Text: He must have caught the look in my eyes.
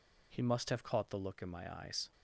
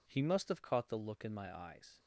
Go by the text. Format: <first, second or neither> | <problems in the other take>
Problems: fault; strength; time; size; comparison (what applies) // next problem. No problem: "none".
neither | none